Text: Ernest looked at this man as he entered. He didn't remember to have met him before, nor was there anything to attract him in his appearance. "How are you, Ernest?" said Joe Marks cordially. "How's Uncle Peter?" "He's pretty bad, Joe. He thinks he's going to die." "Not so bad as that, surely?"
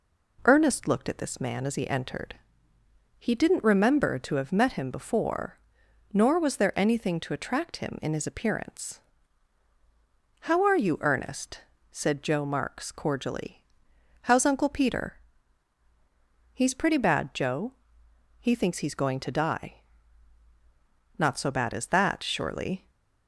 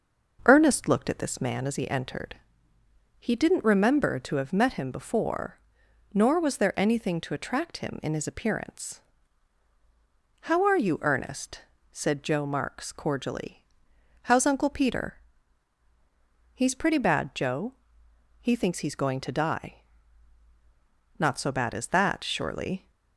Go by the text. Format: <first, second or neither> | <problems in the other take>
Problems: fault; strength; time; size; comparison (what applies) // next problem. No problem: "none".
first | starts louder than the rest; noticeable; until 1.7 s; 5.5 dB